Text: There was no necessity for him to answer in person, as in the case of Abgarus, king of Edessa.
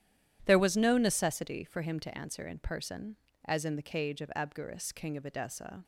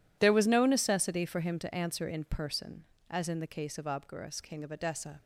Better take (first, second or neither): second